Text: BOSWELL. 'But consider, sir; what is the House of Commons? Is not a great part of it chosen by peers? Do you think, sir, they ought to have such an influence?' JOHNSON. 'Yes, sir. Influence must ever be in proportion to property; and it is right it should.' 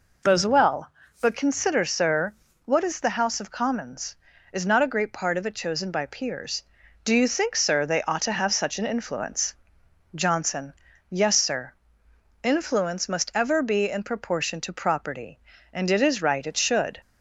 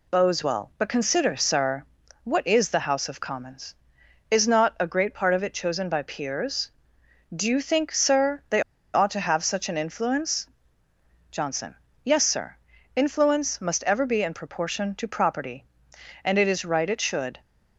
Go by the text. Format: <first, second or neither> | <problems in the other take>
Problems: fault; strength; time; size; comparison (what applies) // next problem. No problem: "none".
first | pauses between "they" and "ought"; slight; at 8.6 s; 0.32 s long